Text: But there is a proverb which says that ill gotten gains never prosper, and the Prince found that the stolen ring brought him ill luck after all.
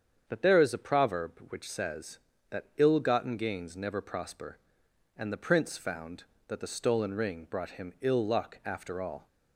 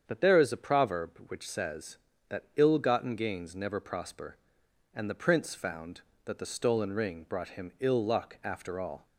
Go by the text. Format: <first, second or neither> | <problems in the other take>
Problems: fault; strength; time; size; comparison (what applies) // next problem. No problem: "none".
neither | starts louder than the rest; strong; the same in both